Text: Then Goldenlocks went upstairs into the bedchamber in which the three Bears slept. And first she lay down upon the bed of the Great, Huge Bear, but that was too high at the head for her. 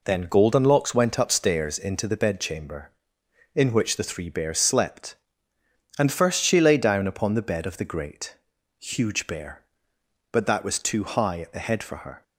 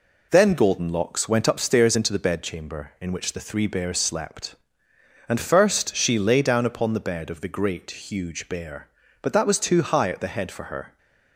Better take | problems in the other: neither | none

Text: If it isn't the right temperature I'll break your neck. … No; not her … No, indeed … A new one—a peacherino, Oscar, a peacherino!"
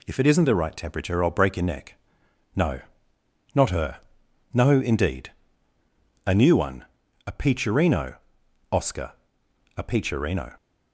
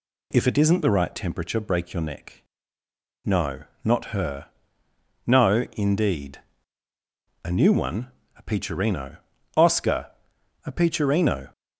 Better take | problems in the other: first | skips "I'll"; at 1.5 s

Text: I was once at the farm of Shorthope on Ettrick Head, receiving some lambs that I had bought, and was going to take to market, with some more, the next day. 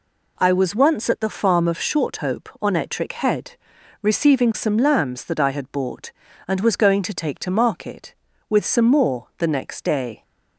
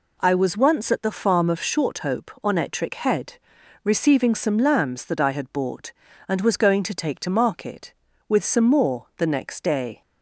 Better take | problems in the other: neither | none

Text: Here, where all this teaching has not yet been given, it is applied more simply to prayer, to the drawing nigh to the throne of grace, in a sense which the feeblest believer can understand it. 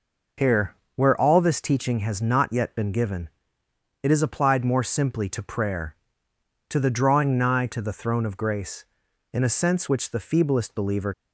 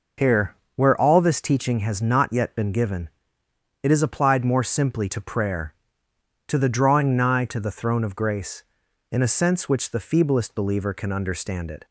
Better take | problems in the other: second | stops before "can understand it"; at 11.1 s

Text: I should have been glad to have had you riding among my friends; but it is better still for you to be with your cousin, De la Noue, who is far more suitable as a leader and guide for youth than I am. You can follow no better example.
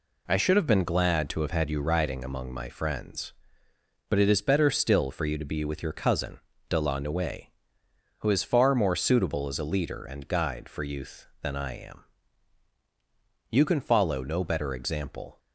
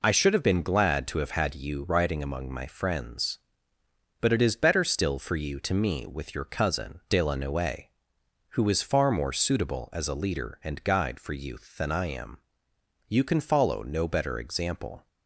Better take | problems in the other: first | says "me" for "be"; at 5.7 s

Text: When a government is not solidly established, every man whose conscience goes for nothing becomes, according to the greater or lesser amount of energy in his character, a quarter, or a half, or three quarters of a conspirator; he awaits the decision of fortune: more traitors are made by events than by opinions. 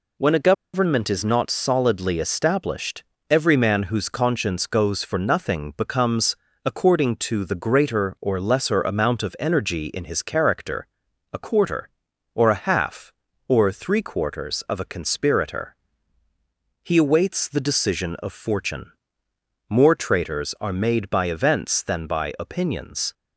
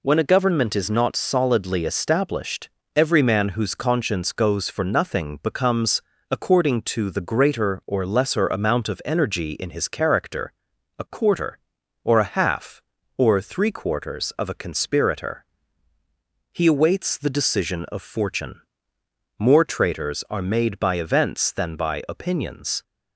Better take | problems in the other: second | pauses between "a" and "government"; slight; at 0.5 s; 0.21 s long

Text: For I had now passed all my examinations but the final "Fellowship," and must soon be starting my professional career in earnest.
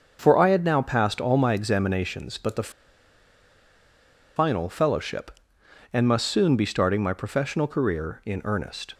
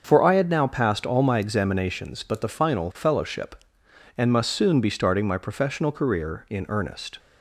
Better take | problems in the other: second | starts louder than the rest; until 1.2 s; 6.5 dB; also in the second // pauses between "the" and "final"; strong; at 2.7 s; 1.6 s long

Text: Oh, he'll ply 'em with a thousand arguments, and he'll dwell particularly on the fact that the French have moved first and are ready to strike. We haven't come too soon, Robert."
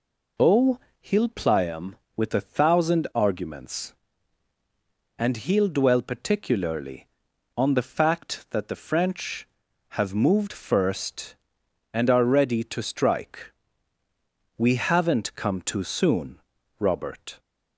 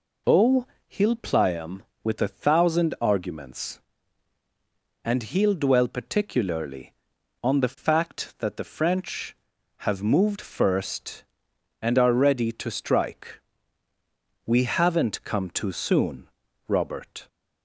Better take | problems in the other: neither | none

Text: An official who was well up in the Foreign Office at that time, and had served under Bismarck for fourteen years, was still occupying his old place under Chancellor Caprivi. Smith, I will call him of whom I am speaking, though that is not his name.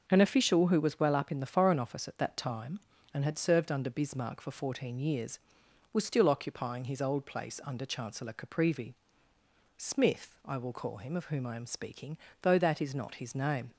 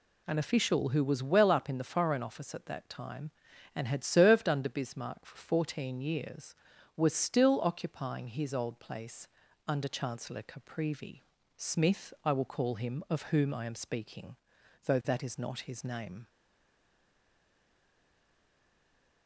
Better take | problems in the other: first | pauses between "place" and "under"; at 9.2 s; 0.40 s long // stays silent after the last word; strong; from 16.2 s on; 3.0 s long

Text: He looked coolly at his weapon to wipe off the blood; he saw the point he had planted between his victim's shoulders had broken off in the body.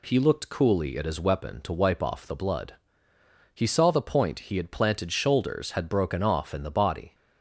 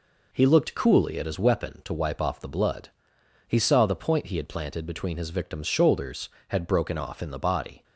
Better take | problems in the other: second | skips "between his victim's"; at 5.1 s

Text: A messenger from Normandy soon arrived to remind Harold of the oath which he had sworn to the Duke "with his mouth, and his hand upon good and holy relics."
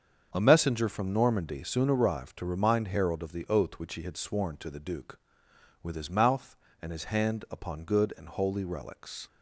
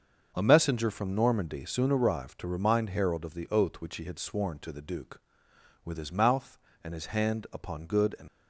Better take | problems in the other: first | starts louder than the rest; until 1.3 s; 6.5 dB; also in the first // stops before "holy relics"; at 8.2 s

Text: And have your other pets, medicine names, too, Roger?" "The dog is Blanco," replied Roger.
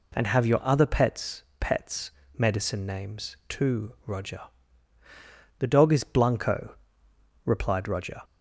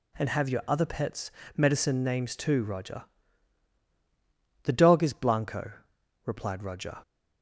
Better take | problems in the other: second | says "pets" twice; at 1.5 s

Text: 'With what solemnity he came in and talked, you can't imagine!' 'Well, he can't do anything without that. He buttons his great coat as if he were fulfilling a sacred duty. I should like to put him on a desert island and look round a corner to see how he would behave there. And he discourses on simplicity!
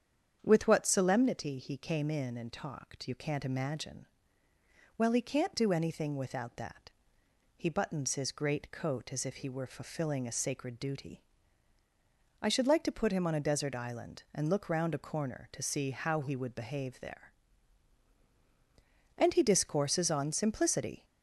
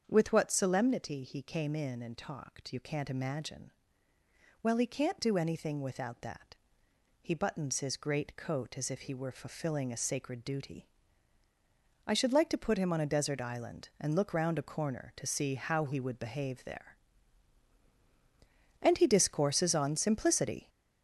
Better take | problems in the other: first | gets louder; noticeable; throughout; 5.5 dB // starts louder than the rest; strong; until 1.0 s; 7.5 dB; strong in the first

